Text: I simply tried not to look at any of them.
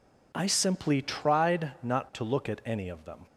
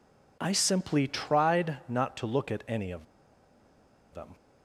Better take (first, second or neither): first